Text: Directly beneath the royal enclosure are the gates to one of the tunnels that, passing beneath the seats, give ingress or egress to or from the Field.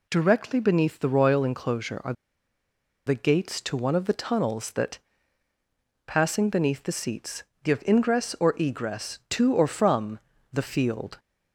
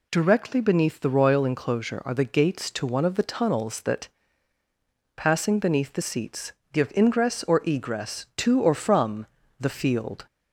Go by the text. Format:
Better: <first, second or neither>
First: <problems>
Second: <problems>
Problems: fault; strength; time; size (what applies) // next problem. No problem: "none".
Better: second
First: pauses between "are" and "the"; noticeable; at 2.1 s; 0.92 s long // pauses between "from" and "the"; slight; at 10.1 s; 0.32 s long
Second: pauses between "from" and "the"; slight; at 9.2 s; 0.32 s long